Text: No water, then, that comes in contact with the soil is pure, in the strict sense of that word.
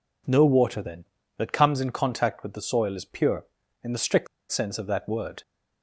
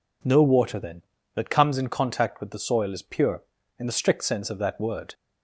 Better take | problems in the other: second | pauses between "strict" and "sense"; slight; at 4.2 s; 0.24 s long

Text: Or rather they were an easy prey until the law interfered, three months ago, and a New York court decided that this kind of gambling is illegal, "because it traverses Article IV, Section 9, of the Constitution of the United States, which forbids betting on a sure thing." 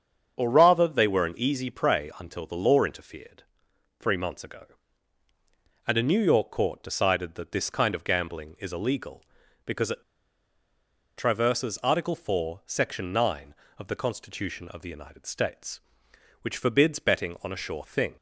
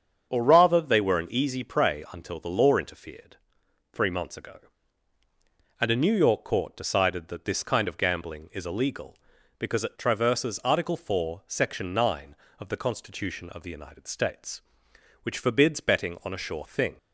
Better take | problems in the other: second | starts louder than the rest; until 1.3 s; 7 dB; also in the second // pauses between "it" and "traverses"; at 10.0 s; 1.1 s long

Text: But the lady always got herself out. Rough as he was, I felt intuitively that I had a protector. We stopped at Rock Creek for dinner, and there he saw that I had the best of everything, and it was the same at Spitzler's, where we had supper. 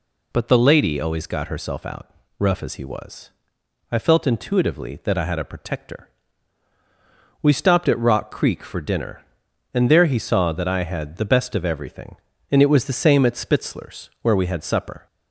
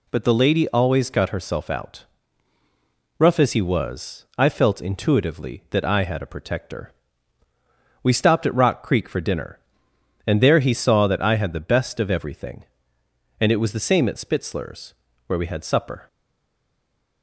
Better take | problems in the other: first | stays silent after the last word; from 16.0 s on; 1.2 s long

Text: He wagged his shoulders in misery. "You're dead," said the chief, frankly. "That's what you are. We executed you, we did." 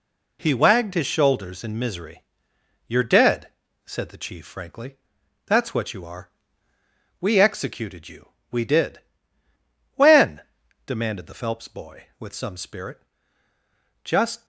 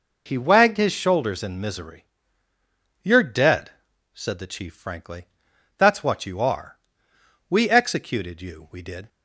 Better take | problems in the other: second | goes on to say "When demanded the Phelps boy with some spirit Just"; strong; from 9.9 s on; 4.5 s long

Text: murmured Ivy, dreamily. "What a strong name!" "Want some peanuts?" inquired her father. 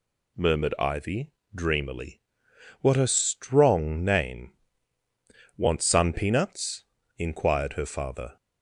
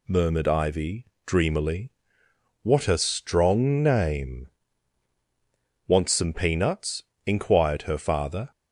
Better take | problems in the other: second | says "sun" for "some"; at 5.8 s

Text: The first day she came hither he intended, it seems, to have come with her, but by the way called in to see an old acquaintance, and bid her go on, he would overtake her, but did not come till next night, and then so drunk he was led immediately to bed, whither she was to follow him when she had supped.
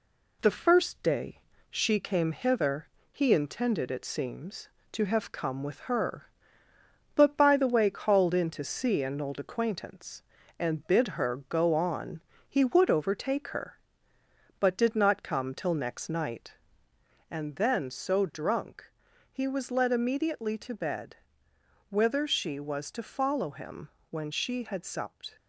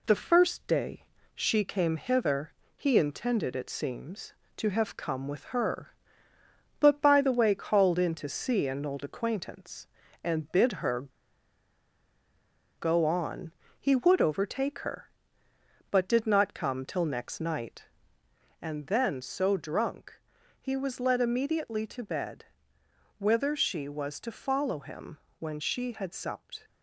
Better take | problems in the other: first | pauses between "day" and "she"; slight; at 1.0 s; 0.30 s long; slight in the first // pauses between "hither" and "he"; slight; at 2.5 s; 0.24 s long; slight in the first // pauses between "her" and "go"; strong; at 11.0 s; 1.7 s long // pauses between "drunk" and "he"; at 20.1 s; 0.40 s long; also in the first // pauses between "him" and "when"; slight; at 25.1 s; 0.20 s long; slight in the first

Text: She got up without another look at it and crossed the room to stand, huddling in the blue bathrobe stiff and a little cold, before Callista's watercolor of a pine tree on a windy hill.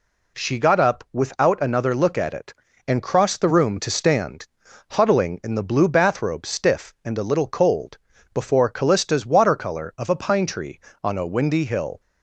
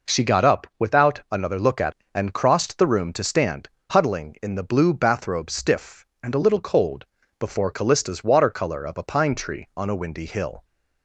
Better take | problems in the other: first | skips "it"; at 2.0 s

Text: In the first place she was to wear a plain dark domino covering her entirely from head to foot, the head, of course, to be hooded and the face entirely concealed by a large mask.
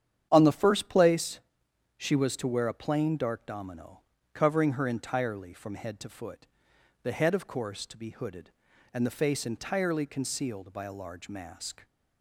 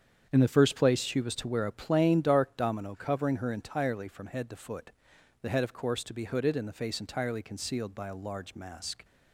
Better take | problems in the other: second | starts louder than the rest; strong; until 1.3 s; 9 dB; strong in the second // says "On" for "In"; at 0.3 s // pauses between "place" and "she"; noticeable; at 1.3 s; 0.58 s long // pauses between "domino" and "covering"; slight; at 3.9 s; 0.34 s long

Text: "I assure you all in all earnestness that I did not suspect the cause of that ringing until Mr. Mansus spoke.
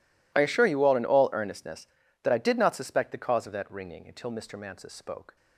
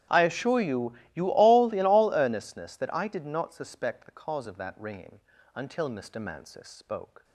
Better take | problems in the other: first | starts louder than the rest; strong; until 1.2 s; 10.5 dB // says "you" twice; at 1.1 s // pauses between "ringing" and "until"; slight; at 5.1 s; 0.34 s long

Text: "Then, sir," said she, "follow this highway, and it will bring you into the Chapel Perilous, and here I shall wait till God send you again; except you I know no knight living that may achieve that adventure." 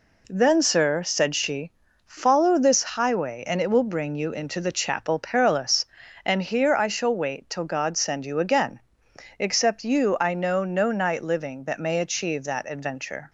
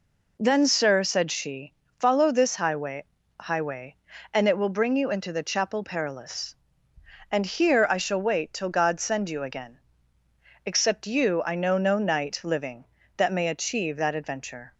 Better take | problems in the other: first | says "highway" twice; at 3.3 s

